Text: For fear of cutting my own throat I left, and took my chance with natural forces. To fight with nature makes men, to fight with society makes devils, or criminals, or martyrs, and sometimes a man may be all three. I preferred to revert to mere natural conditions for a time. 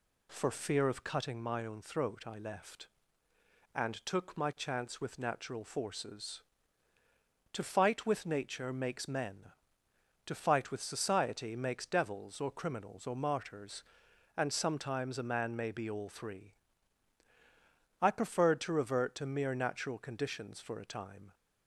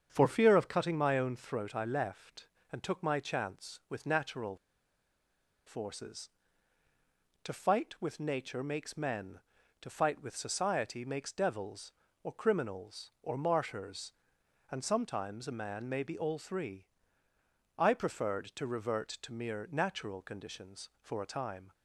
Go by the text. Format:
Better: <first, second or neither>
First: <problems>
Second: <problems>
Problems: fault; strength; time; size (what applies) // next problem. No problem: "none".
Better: first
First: none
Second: starts louder than the rest; strong; until 1.1 s; 7.5 dB // pauses between "natural" and "forces"; at 4.5 s; 1.0 s long